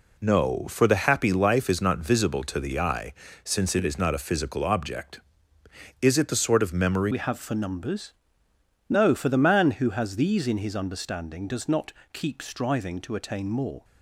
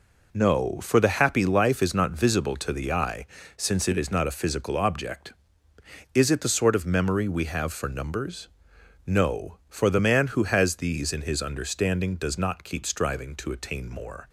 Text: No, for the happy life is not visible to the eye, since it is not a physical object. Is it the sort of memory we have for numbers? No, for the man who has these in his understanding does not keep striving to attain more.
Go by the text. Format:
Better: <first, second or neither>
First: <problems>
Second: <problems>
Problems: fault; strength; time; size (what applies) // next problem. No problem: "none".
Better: second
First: changes voice at "we"; from 7.1 s on; 6.7 s long // pauses between "not" and "keep"; slight; at 11.9 s; 0.20 s long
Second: none